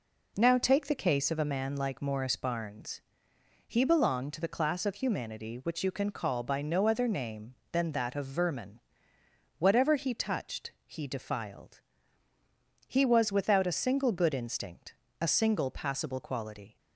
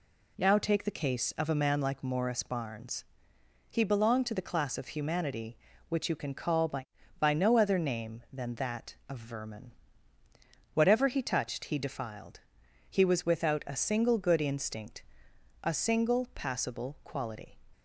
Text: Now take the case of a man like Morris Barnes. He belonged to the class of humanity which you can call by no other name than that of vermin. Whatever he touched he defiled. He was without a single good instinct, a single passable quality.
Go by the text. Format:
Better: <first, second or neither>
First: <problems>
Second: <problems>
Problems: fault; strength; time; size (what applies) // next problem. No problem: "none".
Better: first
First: none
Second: says "by" twice; at 7.2 s